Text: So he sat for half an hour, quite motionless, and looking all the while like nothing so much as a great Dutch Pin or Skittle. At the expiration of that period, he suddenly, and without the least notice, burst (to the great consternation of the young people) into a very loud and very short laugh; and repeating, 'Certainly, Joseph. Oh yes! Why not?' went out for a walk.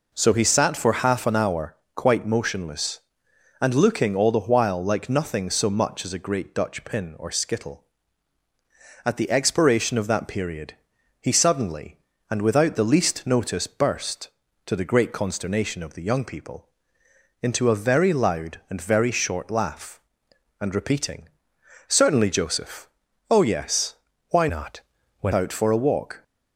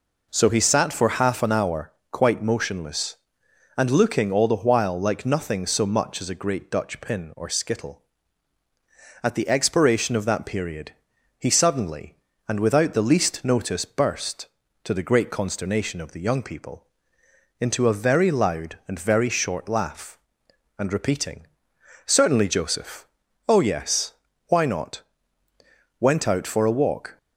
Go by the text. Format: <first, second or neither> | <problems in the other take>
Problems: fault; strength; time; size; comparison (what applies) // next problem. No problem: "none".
second | changes voice from "not" to "went"; from 24.4 to 25.3 s; 0.9 s long